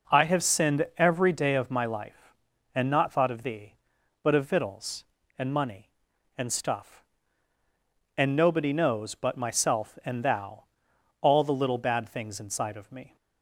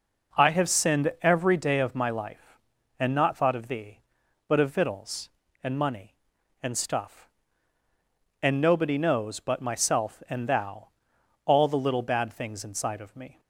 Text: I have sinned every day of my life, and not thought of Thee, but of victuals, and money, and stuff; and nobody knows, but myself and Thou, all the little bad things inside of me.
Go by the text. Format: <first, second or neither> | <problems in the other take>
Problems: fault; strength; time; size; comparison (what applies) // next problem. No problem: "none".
neither | none